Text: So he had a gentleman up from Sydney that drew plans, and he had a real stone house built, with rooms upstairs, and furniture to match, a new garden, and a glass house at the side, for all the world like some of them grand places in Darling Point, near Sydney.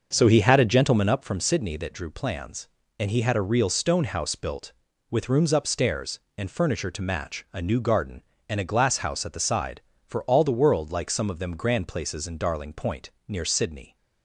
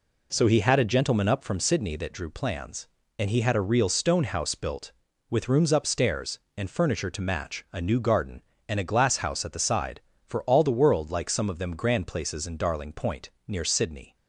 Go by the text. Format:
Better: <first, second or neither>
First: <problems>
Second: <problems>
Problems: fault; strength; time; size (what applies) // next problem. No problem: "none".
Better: second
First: starts louder than the rest; until 1.1 s; 6.5 dB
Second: none